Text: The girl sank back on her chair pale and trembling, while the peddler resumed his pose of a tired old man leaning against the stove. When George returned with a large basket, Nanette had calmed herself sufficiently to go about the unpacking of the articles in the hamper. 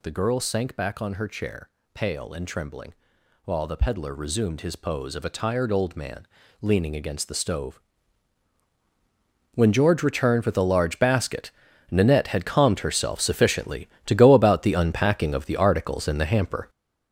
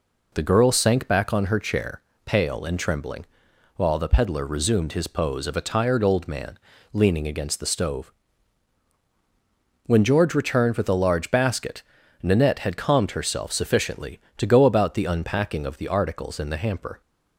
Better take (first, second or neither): second